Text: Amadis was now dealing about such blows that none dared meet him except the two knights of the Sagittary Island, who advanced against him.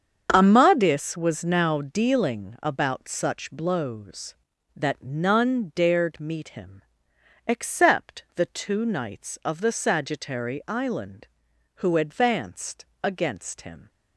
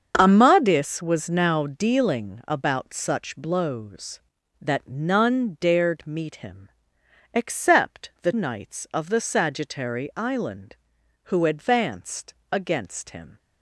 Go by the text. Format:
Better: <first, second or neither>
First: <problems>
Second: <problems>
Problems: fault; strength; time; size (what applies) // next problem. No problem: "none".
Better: first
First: starts louder than the rest; strong; until 1.3 s; 7.5 dB // pauses between "him" and "except"; noticeable; at 6.8 s; 0.64 s long // pauses between "advanced" and "against"; slight; at 12.8 s; 0.18 s long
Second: starts louder than the rest; until 1.1 s; 7 dB // pauses between "him" and "except"; noticeable; at 6.6 s; 0.64 s long // skips "two"; at 8.3 s // pauses between "advanced" and "against"; slight; at 12.3 s; 0.18 s long